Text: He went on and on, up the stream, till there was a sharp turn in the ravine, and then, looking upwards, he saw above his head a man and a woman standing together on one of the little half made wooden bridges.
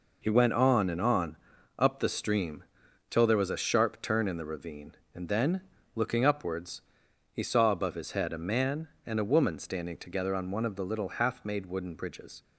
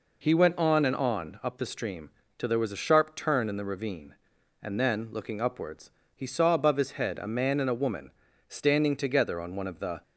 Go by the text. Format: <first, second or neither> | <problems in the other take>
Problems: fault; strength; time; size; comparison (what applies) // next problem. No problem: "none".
first | pauses between "woman" and "standing"; slight; at 8.1 s; 0.36 s long // stops before "little half made wooden bridges"; at 10.0 s